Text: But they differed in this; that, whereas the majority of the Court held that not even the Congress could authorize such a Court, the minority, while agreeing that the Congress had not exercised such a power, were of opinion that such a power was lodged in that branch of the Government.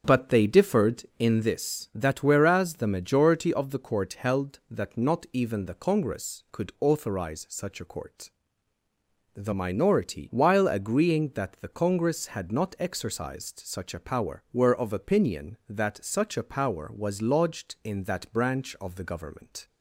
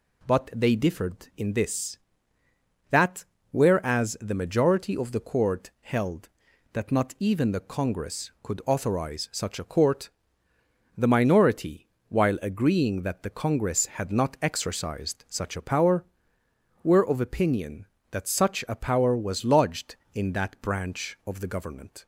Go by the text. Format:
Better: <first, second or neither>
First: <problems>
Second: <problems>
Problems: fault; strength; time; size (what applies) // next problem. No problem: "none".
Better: second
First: starts louder than the rest; strong; until 1.5 s; 7.5 dB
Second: none